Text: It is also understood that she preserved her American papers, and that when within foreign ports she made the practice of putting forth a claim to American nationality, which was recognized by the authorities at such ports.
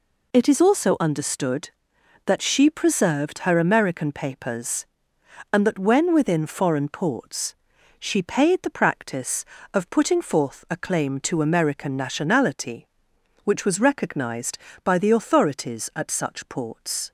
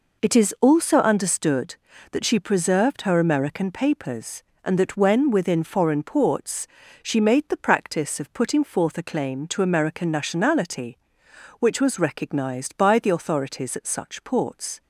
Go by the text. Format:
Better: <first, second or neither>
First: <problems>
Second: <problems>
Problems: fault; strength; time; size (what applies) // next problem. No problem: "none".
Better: second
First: pauses between "ports" and "she"; at 7.5 s; 0.42 s long // says "paid" for "made"; at 8.2 s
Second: pauses between "ports" and "she"; slight; at 6.6 s; 0.34 s long